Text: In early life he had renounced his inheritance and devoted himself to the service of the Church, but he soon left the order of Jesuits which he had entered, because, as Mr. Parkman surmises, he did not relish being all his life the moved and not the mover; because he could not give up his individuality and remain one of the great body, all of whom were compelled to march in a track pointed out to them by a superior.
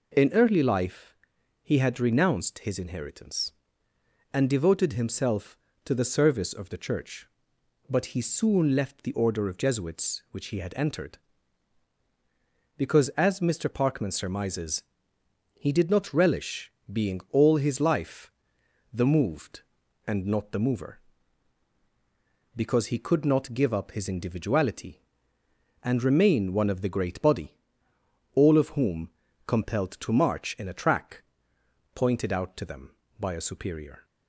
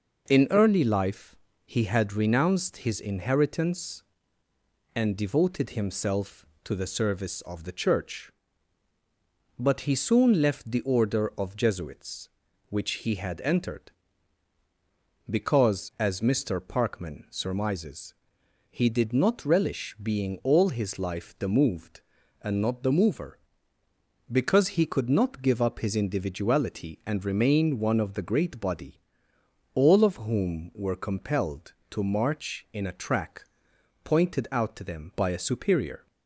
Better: second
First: pauses between "life" and "he"; noticeable; at 1.1 s; 0.48 s long // pauses between "relish" and "being"; slight; at 16.7 s; 0.20 s long // pauses between "life" and "the"; noticeable; at 18.3 s; 0.62 s long // skips "were"; at 29.2 s // pauses between "track" and "pointed"; noticeable; at 31.2 s; 0.72 s long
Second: pauses between "life" and "he"; slight; at 1.3 s; 0.28 s long // pauses between "track" and "pointed"; noticeable; at 33.4 s; 0.62 s long

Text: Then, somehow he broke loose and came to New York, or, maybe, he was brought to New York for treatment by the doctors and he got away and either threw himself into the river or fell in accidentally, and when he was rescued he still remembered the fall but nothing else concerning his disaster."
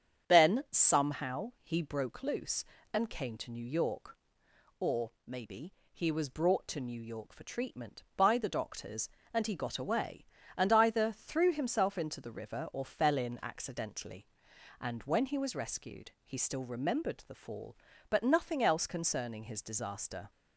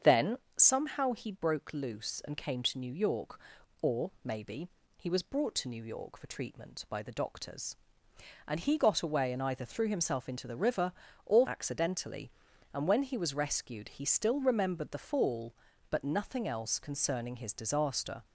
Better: first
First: starts louder than the rest; strong; until 1.3 s; 8 dB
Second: starts louder than the rest; strong; until 1.2 s; 7.5 dB // skips "fell in"; at 11.4 s

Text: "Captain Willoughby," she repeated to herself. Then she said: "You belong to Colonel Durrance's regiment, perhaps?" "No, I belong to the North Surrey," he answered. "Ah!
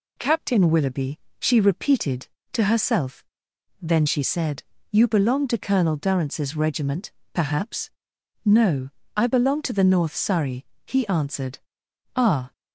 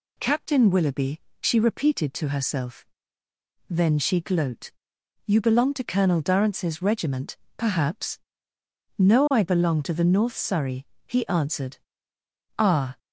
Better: first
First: none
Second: says "gloat" for "said"; at 4.1 s

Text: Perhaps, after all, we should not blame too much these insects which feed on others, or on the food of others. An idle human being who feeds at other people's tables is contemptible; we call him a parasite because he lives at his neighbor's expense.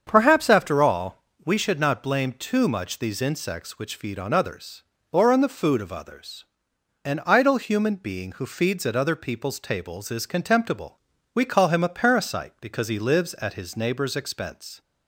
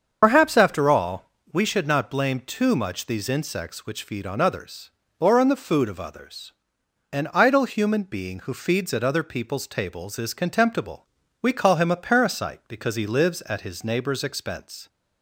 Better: first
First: starts louder than the rest; strong; until 1.0 s; 7.5 dB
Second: loses the start of "Perhaps"; at 0.2 s; 80 ms // starts louder than the rest; until 1.2 s; 7 dB

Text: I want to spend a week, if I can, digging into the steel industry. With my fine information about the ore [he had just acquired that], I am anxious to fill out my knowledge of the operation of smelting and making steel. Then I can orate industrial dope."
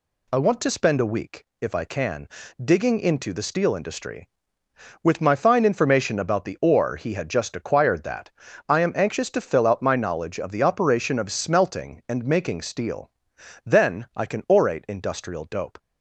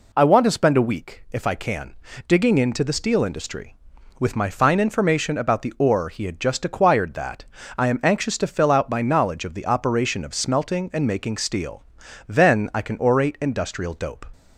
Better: neither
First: none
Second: none

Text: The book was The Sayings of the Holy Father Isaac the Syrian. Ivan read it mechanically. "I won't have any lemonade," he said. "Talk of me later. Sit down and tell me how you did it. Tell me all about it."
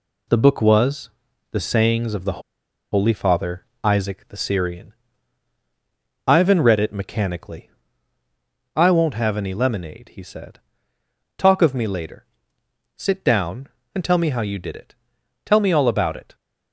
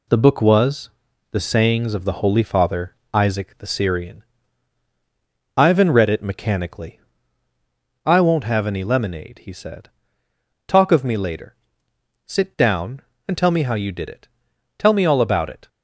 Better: second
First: pauses between "was" and "The"; at 1.0 s; 0.44 s long // pauses between "the" and "Holy"; noticeable; at 2.4 s; 0.51 s long // pauses between "Father" and "Isaac"; slight; at 3.6 s; 0.18 s long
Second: pauses between "was" and "The"; at 0.8 s; 0.44 s long // pauses between "Father" and "Isaac"; slight; at 2.9 s; 0.18 s long

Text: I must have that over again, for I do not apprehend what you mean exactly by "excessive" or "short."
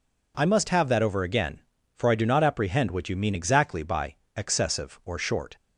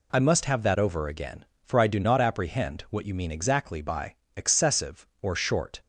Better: neither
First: pauses between "by" and "excessive"; slight; at 4.1 s; 0.18 s long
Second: pauses between "by" and "excessive"; slight; at 4.1 s; 0.20 s long

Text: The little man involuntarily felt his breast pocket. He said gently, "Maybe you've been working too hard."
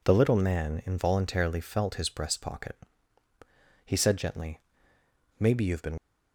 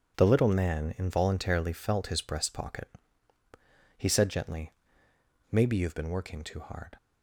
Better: second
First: stops before "working too hard"; at 5.9 s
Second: none

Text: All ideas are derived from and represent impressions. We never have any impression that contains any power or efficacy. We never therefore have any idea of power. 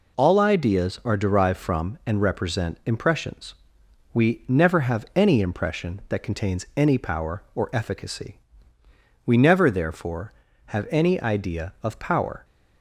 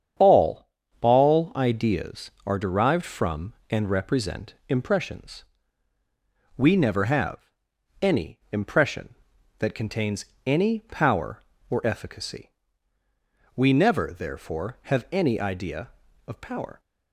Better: first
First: none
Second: starts louder than the rest; strong; until 1.5 s; 8 dB // says "All" twice; at 0.9 s // pauses between "have" and "any"; noticeable; at 7.3 s; 0.66 s long // pauses between "contains" and "any"; slight; at 10.2 s; 0.18 s long

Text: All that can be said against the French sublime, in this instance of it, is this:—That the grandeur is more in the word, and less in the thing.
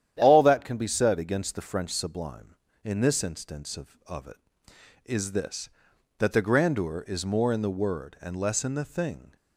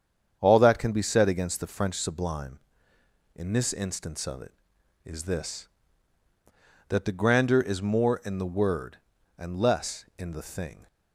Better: second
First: starts louder than the rest; strong; until 1.1 s; 10 dB // says "of" twice; at 4.0 s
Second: starts louder than the rest; strong; until 1.4 s; 7.5 dB

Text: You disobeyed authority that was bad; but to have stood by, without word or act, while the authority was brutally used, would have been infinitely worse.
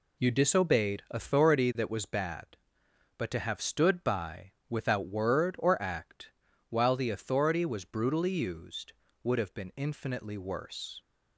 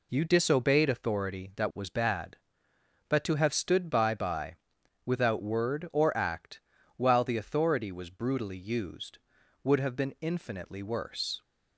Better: first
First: none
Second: says "by" twice; at 4.1 s

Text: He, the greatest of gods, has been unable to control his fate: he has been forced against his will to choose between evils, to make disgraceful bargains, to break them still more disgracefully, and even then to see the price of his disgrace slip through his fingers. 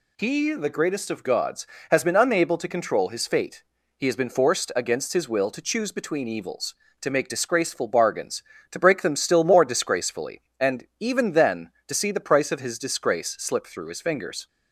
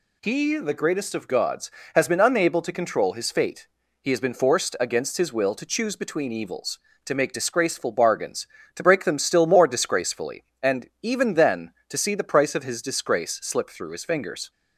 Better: neither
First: none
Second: none

